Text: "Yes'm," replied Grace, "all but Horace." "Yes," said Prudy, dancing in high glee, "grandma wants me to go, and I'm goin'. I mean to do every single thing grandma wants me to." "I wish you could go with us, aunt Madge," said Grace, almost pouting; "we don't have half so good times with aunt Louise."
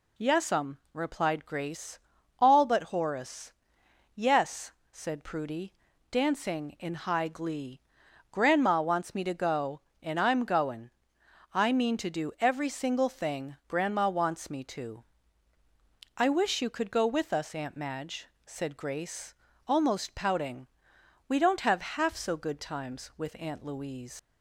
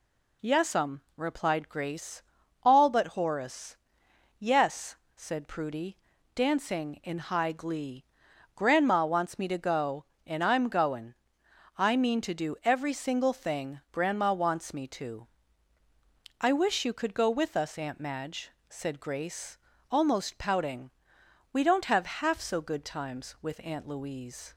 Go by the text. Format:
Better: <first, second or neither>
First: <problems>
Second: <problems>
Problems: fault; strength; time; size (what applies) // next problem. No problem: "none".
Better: second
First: leaves "Louise" unfinished; at 24.1 s; 120 ms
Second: none